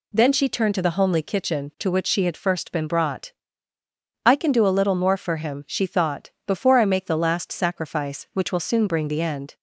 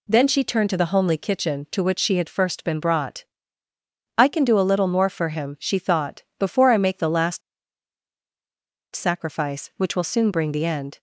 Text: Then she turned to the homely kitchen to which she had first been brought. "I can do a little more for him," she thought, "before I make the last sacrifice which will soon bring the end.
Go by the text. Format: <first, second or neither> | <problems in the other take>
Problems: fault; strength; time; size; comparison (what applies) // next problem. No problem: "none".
first | pauses between "last" and "sacrifice"; strong; at 7.4 s; 1.5 s long